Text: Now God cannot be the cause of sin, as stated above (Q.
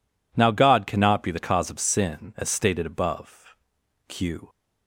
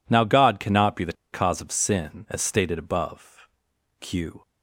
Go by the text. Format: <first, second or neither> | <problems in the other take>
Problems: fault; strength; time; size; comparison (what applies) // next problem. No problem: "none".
first | pauses between "the" and "cause"; slight; at 1.1 s; 0.18 s long